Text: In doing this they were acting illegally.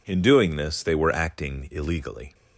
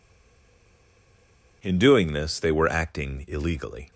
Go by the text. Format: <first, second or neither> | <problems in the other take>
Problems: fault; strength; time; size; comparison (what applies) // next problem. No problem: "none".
first | stays silent before the first word; noticeable; until 1.6 s; 1.6 s long